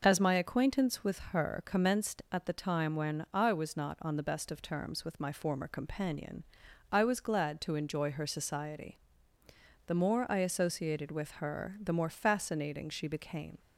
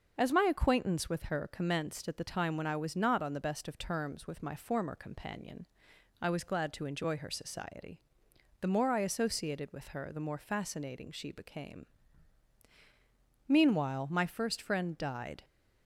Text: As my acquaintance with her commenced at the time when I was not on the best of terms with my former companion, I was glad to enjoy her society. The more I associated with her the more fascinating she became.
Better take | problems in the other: first | starts louder than the rest; noticeable; until 1.1 s; 6 dB // goes on to say "Meanwhile my first friend died"; strong; from 13.4 s on; 1.9 s long

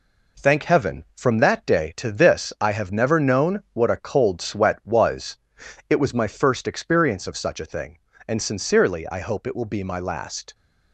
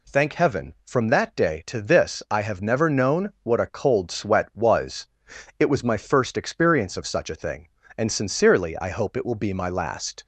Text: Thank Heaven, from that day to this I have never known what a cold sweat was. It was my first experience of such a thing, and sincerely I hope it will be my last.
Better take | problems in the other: second | gets quieter; noticeable; throughout; 5 dB

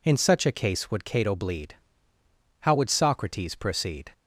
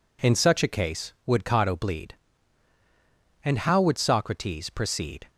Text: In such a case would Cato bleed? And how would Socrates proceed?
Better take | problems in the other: second | skips "And"; at 2.1 s

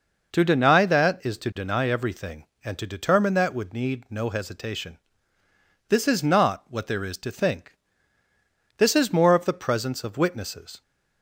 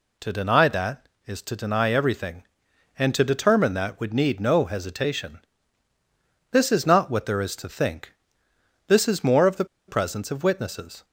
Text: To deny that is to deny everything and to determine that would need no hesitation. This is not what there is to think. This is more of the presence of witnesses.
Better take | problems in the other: first | pauses between "the" and "presence"; slight; at 9.6 s; 0.22 s long

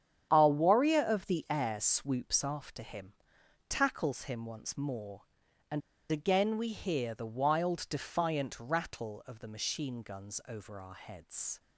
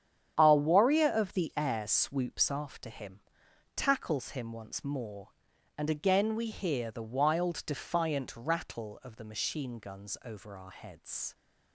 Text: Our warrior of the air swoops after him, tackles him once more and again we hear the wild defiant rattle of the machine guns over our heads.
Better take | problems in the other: second | starts louder than the rest; strong; until 1.3 s; 9 dB; strong in the second // pauses between "and" and "again"; slight; at 5.8 s; 0.30 s long

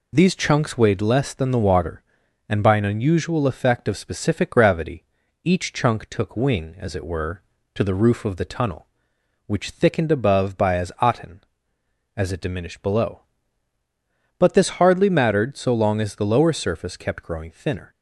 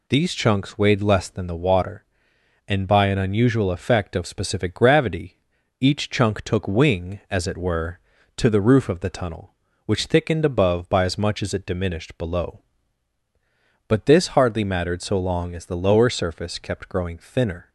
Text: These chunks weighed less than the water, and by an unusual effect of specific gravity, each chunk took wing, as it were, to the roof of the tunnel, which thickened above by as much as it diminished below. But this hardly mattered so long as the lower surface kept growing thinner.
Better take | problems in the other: second | says "aten" for "much"; at 11.0 s

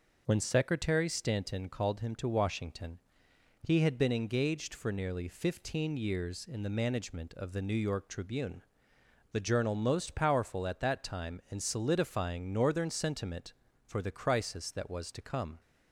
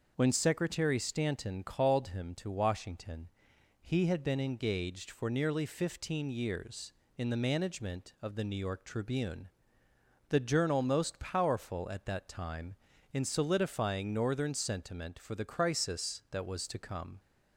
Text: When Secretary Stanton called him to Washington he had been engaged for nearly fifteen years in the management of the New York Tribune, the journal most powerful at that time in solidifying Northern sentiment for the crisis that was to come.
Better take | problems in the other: neither | pauses between "Washington" and "he"; noticeable; the same in both

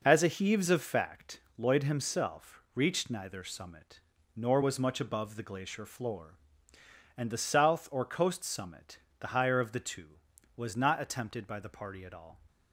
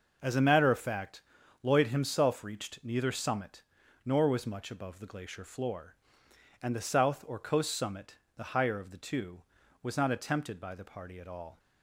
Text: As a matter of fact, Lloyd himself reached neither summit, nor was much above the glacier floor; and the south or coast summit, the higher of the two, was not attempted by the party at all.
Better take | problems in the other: second | says "heaves" for "matter"; at 0.2 s

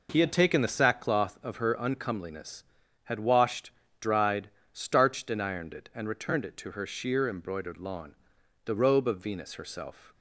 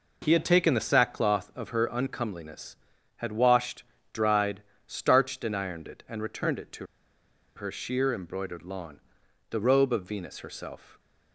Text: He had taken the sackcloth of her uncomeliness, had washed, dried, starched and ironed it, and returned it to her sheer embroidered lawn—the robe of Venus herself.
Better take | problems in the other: first | pauses between "to" and "her"; noticeable; at 6.8 s; 0.70 s long

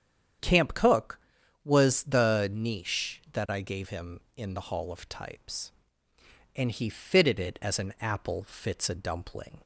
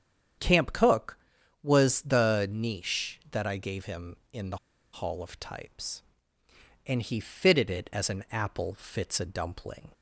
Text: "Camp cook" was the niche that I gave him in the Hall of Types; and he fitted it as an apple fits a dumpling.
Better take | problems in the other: first | starts louder than the rest; strong; until 1.8 s; 8.5 dB; strong in the first // pauses between "the" and "Hall"; slight; at 4.5 s; 0.35 s long

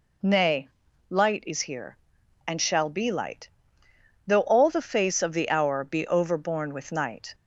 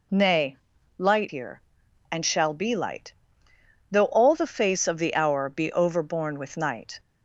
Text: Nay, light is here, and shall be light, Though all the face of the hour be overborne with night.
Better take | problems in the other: first | skips "is"; at 1.2 s

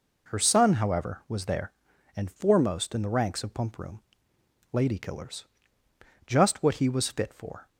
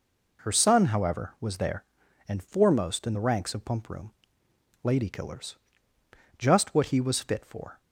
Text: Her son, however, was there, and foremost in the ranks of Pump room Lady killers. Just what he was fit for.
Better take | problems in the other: neither | pauses between "room" and "Lady"; noticeable; the same in both

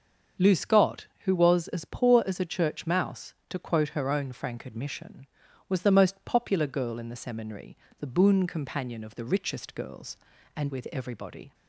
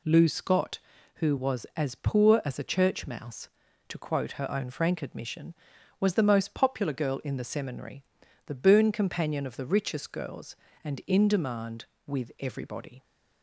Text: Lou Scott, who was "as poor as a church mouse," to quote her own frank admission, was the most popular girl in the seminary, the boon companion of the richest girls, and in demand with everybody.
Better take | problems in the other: second | starts louder than the rest; until 1.5 s; 7 dB // skips "in demand"; at 10.6 s

